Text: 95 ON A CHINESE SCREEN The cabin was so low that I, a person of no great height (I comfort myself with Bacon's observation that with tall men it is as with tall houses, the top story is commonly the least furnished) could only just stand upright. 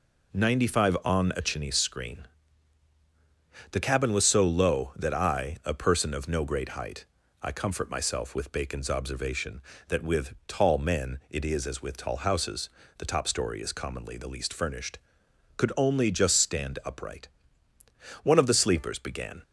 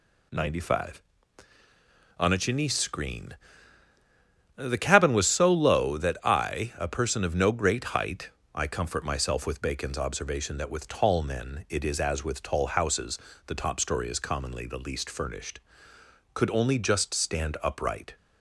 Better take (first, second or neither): second